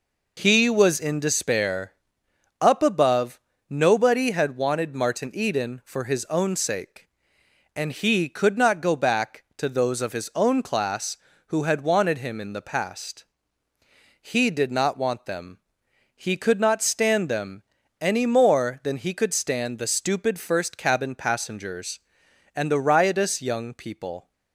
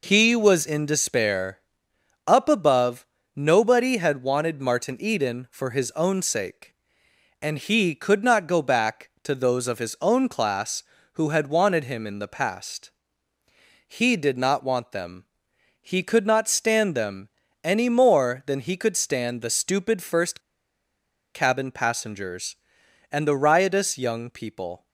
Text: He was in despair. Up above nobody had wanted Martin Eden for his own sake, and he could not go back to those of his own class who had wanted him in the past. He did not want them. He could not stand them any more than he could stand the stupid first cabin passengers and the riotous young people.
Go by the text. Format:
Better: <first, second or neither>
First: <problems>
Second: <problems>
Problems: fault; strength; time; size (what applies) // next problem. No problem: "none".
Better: first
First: pauses between "above" and "nobody"; slight; at 3.3 s; 0.28 s long // pauses between "them" and "any"; at 17.6 s; 0.37 s long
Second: pauses between "above" and "nobody"; slight; at 3.0 s; 0.28 s long // pauses between "them" and "any"; slight; at 17.3 s; 0.34 s long // pauses between "first" and "cabin"; noticeable; at 20.3 s; 0.96 s long